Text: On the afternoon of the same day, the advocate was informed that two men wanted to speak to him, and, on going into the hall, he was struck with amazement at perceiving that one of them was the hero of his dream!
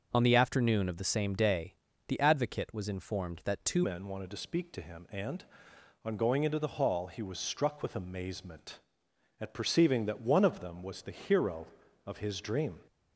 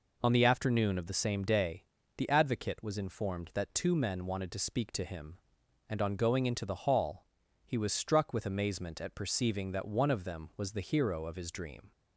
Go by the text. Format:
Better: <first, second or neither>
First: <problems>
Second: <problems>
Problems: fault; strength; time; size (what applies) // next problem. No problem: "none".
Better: second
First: starts louder than the rest; until 1.1 s; 6.5 dB // changes voice at "men"; from 3.8 s on; 8.9 s long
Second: none